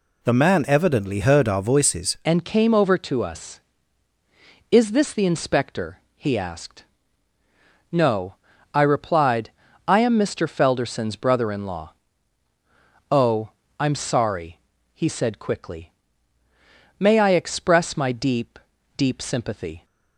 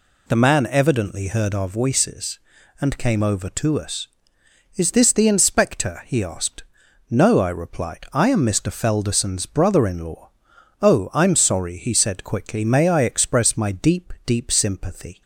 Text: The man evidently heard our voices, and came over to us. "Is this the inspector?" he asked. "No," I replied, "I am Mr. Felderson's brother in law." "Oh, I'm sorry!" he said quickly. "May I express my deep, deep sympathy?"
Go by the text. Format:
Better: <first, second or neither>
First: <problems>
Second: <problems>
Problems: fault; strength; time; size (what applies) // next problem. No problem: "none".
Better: second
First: changes voice at "and"; from 2.2 s on; 17.6 s long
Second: none